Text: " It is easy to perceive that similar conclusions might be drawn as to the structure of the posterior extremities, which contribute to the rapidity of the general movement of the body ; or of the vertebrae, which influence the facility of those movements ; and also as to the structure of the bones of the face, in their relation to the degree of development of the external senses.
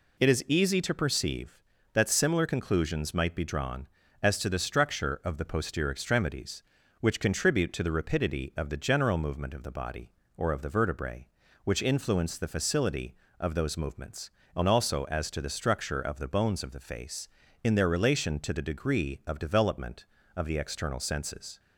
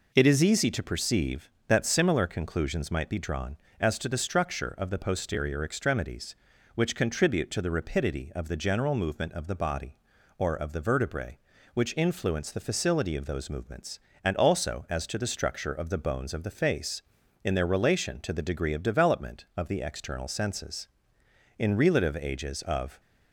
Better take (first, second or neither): first